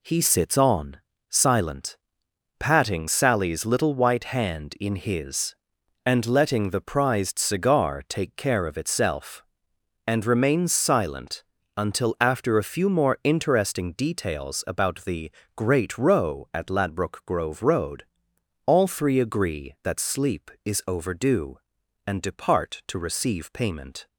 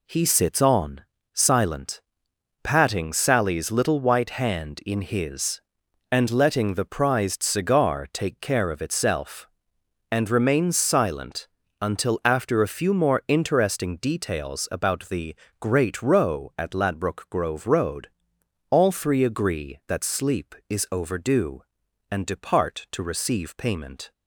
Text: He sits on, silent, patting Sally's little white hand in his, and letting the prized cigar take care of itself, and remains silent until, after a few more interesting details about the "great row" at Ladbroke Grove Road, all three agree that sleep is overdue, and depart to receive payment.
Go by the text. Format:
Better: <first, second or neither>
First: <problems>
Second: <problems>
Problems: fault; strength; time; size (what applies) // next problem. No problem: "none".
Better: neither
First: pauses between "silent" and "until"; slight; at 11.4 s; 0.32 s long // pauses between "the" and "great"; slight; at 15.3 s; 0.26 s long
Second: pauses between "silent" and "until"; slight; at 11.4 s; 0.32 s long // pauses between "the" and "great"; slight; at 15.3 s; 0.26 s long